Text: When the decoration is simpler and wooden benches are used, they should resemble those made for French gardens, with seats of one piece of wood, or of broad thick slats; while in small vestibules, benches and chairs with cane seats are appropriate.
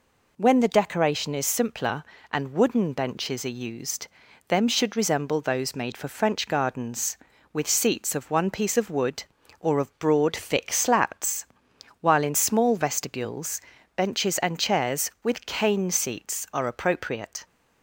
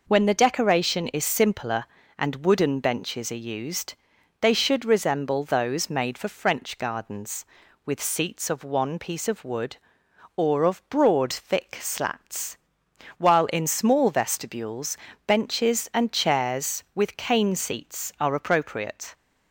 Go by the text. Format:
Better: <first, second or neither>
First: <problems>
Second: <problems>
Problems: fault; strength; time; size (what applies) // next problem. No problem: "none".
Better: second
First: says "them" for "they"; at 4.4 s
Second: none